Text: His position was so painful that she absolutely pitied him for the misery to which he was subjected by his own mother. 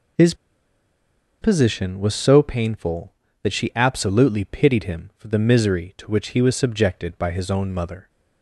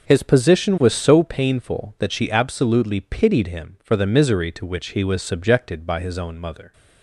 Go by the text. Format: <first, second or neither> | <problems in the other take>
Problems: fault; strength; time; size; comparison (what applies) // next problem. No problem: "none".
second | pauses between "His" and "position"; at 0.3 s; 1.0 s long